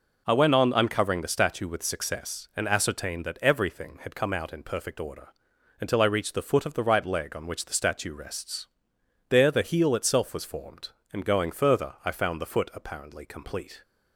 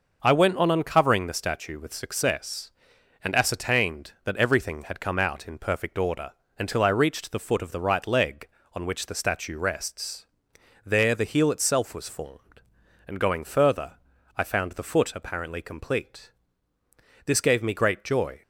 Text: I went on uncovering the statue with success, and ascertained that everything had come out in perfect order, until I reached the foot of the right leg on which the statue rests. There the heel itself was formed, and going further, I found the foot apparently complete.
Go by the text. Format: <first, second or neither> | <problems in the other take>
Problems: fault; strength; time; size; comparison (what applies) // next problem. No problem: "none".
first | goes on to say "This gave me great joy"; noticeable; from 17.2 s on; 1.1 s long